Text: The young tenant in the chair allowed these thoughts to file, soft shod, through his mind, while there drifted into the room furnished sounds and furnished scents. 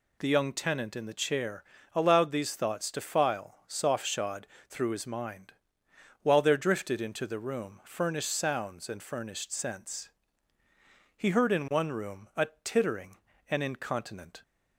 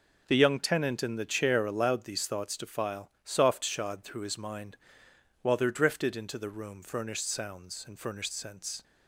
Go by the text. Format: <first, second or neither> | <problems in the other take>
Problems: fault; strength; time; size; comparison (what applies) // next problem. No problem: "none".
second | pauses between "chair" and "allowed"; slight; at 1.6 s; 0.32 s long // goes on to say "He heard in one room a tittering and incontinent"; strong; from 11.1 s on; 3.2 s long